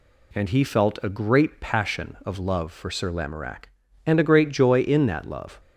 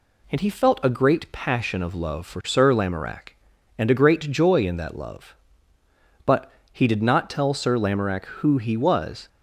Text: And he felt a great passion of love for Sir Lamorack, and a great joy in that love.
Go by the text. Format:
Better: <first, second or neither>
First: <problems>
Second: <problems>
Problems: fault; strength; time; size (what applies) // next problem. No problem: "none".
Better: first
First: none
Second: goes on to say "But he did not tell Sir Lamorack who he was"; strong; from 6.2 s on; 3.0 s long